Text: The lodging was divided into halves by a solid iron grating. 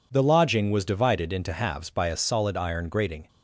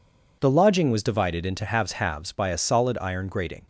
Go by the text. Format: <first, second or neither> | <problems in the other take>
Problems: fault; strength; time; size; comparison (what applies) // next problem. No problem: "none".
first | says "halves" twice; at 1.9 s